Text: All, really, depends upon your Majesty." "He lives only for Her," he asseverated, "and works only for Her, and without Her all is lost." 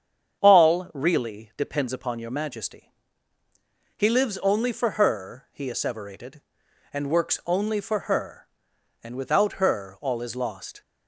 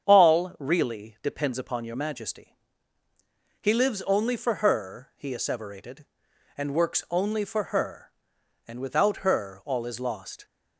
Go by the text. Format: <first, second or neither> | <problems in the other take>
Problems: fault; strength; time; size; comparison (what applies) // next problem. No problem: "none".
neither | starts louder than the rest; strong; the same in both